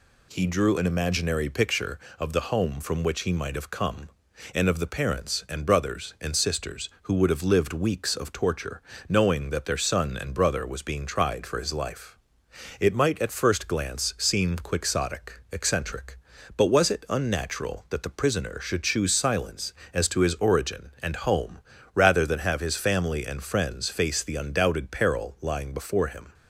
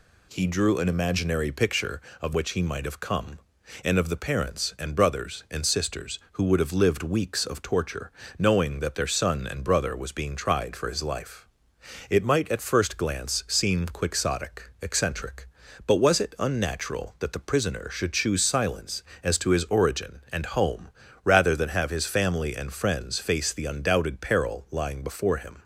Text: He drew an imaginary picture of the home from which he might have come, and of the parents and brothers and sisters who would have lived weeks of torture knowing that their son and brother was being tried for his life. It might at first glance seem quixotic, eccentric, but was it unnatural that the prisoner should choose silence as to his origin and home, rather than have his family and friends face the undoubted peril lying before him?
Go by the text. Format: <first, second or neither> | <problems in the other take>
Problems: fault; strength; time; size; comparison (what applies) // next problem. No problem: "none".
first | skips "the home from"; at 2.3 s // pauses between "torture" and "knowing"; slight; at 8.1 s; 0.28 s long; slight in the first